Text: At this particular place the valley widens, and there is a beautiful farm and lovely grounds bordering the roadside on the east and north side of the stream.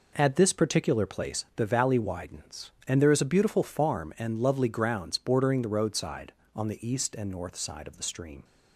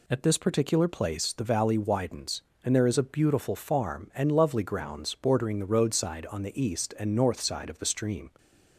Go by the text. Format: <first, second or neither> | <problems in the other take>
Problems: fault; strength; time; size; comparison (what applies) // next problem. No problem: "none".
second | starts louder than the rest; noticeable; until 1.3 s; 4.5 dB